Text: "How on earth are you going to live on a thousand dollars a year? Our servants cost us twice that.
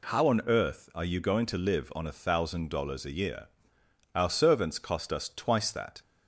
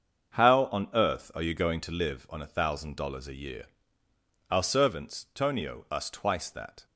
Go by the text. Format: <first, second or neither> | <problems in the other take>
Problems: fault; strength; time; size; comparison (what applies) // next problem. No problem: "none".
first | starts louder than the rest; until 1.5 s; 6.5 dB // says "tonio" for "cost"; at 5.3 s